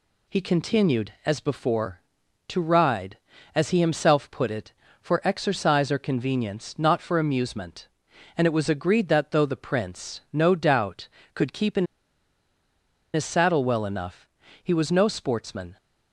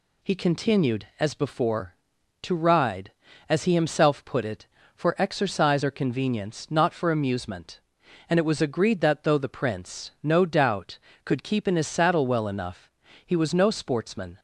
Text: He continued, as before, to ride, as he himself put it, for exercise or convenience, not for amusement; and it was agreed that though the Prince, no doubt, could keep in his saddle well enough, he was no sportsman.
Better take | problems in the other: second | pauses between "in" and "his"; strong; at 11.8 s; 1.2 s long

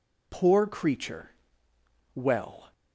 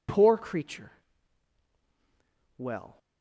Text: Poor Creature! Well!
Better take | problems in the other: neither | none

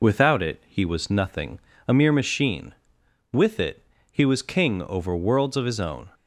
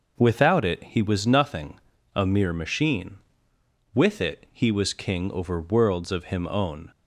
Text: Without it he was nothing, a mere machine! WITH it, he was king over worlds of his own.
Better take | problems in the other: first | says "him" for "his"; at 6.2 s

